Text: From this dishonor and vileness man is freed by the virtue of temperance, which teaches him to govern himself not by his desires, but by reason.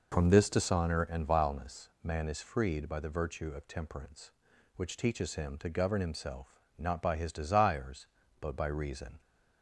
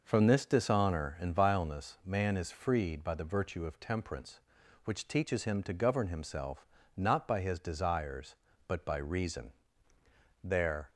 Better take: first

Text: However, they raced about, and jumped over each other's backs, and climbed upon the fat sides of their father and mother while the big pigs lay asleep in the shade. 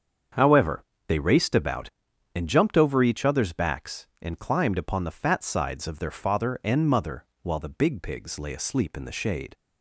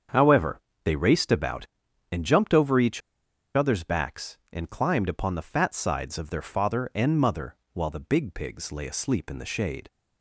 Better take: first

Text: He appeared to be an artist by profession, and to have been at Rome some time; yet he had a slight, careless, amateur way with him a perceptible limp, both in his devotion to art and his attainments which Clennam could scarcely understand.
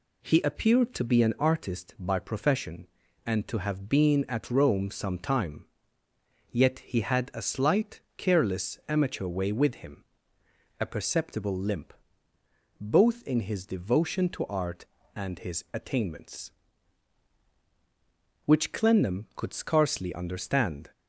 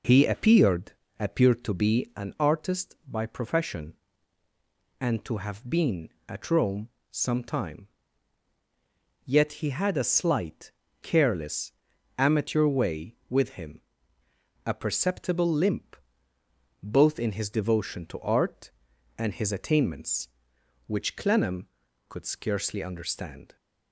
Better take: first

